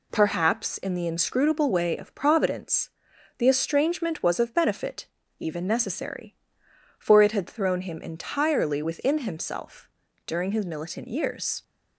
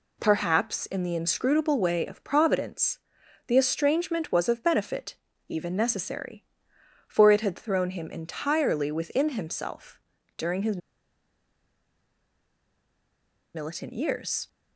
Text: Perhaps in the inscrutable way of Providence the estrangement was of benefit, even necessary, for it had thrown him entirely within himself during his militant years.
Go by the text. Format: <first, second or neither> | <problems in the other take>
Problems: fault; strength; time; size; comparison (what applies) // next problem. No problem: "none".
first | pauses between "Providence" and "the"; noticeable; at 2.9 s; 0.50 s long; noticeable in the first // pauses between "himself" and "during"; at 9.9 s; 0.38 s long; also in the first // pauses between "his" and "militant"; strong; at 10.7 s; 2.7 s long